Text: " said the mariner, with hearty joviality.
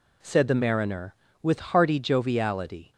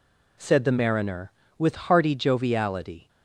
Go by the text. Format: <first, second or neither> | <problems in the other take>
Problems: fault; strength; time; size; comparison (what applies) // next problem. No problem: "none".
neither | none